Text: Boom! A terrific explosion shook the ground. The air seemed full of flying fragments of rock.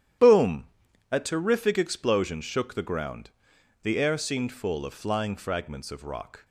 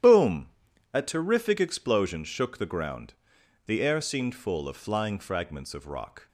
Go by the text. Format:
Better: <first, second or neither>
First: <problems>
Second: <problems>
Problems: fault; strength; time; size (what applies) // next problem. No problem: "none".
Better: neither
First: starts louder than the rest; strong; until 1.6 s; 10.5 dB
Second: starts louder than the rest; strong; until 1.4 s; 10.5 dB